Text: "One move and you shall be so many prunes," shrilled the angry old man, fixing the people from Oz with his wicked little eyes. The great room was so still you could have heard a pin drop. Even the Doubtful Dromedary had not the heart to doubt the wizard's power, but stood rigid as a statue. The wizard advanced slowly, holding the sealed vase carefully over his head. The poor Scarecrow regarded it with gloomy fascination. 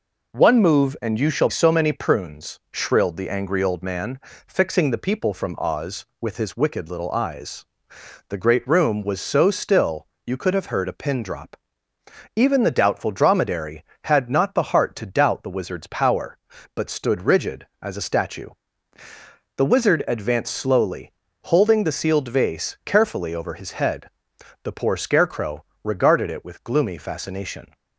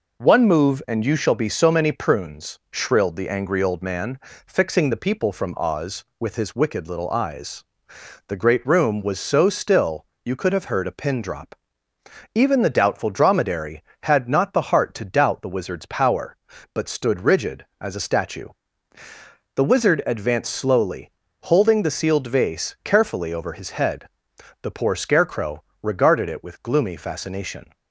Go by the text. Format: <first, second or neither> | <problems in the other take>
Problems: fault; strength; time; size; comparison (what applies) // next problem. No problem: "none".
second | skips "be"; at 1.4 s // pauses between "still" and "you"; slight; at 10.0 s; 0.18 s long; slight in the second // pauses between "Scarecrow" and "regarded"; slight; at 25.6 s; 0.18 s long; slight in the second